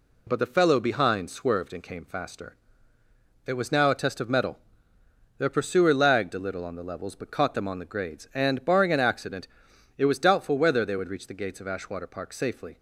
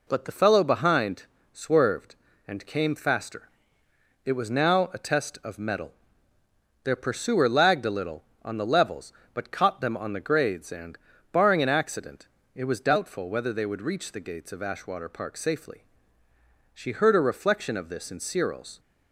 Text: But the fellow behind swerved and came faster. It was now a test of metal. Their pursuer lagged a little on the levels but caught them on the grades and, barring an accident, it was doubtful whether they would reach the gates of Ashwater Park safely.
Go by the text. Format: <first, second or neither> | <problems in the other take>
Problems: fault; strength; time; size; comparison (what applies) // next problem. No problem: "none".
first | pauses between "behind" and "swerved"; slight; at 1.2 s; 0.30 s long // goes on to say "She heard a reflection of this in Cyril's"; strong; from 16.7 s on; 2.0 s long